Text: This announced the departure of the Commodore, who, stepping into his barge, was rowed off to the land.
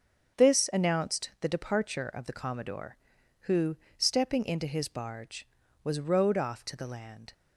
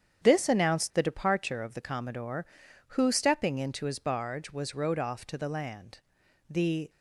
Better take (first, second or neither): first